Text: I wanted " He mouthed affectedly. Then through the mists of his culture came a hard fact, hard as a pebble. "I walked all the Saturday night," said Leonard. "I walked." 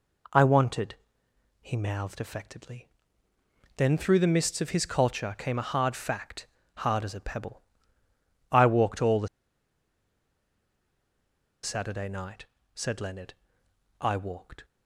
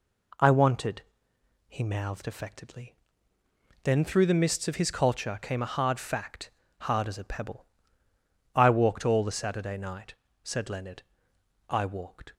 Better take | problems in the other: second | pauses between "the" and "Saturday"; strong; at 9.2 s; 2.3 s long

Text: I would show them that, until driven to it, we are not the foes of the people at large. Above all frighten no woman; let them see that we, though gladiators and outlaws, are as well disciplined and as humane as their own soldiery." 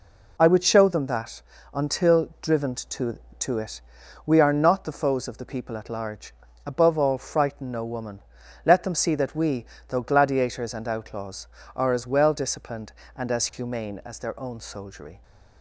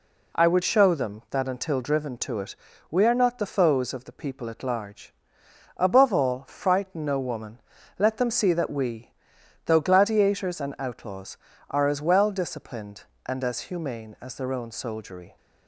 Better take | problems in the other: second | says "to" twice; at 3.3 s

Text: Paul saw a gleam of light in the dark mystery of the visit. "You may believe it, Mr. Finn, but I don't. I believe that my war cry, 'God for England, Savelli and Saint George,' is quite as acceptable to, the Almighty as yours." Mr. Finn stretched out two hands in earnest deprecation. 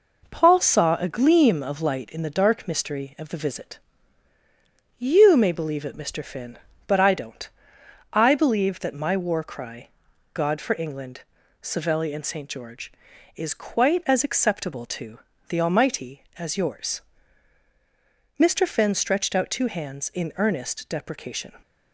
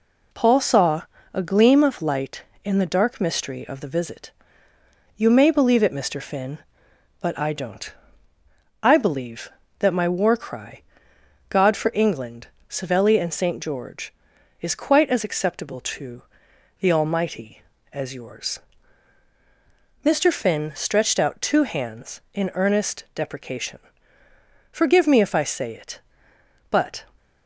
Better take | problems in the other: first | pauses between "saw" and "a"; slight; at 1.0 s; 0.30 s long // goes on to say "Forgive me if I say it but"; strong; from 24.7 s on; 2.3 s long

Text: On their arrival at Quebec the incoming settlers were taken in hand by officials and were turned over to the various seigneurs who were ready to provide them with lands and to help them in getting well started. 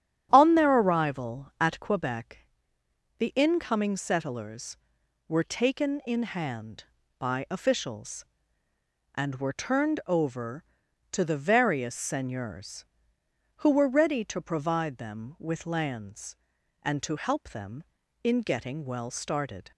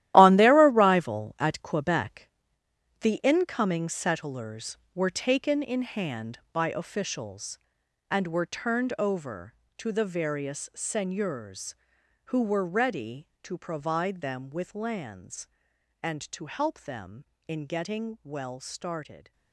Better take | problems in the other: first | gets quieter; strong; throughout; 12 dB // starts louder than the rest; strong; until 1.1 s; 14 dB; strong in the first // pauses between "Quebec" and "the"; noticeable; at 2.2 s; 0.72 s long; noticeable in the first

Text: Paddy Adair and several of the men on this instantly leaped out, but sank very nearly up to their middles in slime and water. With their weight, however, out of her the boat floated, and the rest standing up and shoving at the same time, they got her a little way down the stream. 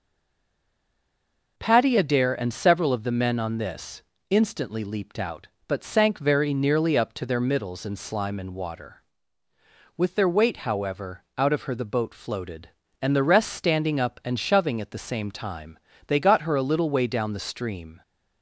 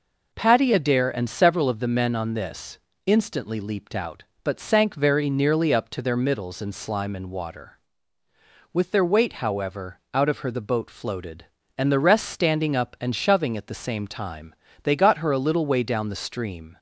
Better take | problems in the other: second | stays silent before the first word; noticeable; until 1.5 s; 1.5 s long // pauses between "this" and "instantly"; slight; at 4.0 s; 0.28 s long; slight in the second

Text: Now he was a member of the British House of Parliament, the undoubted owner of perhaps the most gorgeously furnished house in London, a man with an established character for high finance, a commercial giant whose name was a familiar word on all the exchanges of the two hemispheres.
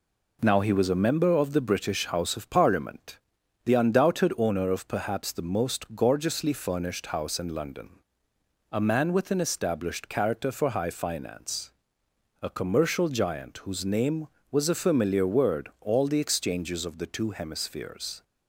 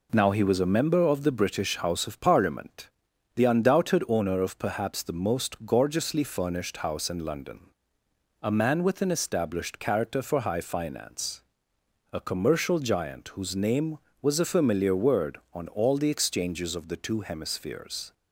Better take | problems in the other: second | skips "on"; at 15.7 s

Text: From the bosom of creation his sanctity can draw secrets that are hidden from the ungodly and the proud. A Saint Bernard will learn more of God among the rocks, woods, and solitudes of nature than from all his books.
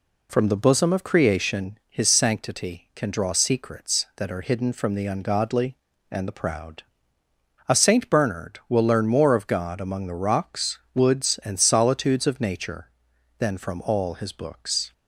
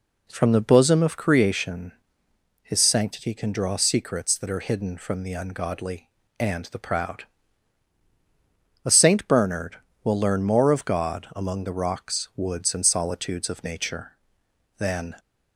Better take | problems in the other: first | pauses between "creation" and "his"; noticeable; at 1.9 s; 0.70 s long // stops before "from all his books"; at 15.1 s

